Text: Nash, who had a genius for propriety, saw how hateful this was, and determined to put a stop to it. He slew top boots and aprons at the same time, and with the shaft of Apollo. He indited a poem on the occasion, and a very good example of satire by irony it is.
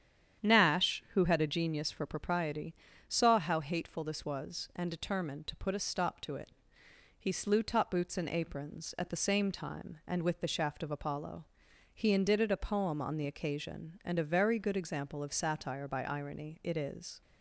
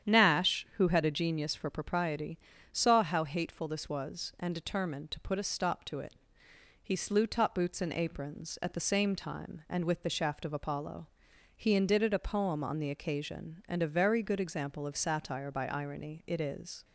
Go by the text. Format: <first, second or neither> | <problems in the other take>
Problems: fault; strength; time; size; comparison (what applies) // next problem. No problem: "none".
neither | starts louder than the rest; strong; the same in both